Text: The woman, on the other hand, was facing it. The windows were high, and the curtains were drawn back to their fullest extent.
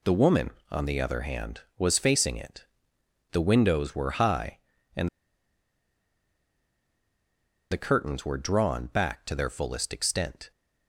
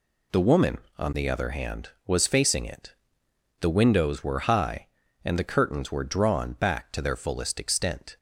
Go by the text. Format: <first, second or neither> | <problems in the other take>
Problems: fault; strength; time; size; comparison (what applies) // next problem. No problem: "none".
second | pauses between "and" and "the"; strong; at 5.0 s; 2.6 s long